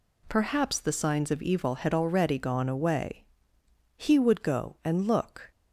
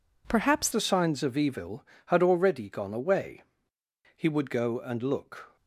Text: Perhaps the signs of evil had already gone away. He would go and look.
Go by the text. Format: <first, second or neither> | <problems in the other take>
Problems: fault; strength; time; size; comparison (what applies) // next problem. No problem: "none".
first | changes voice at "the"; from 0.7 s on; 4.8 s long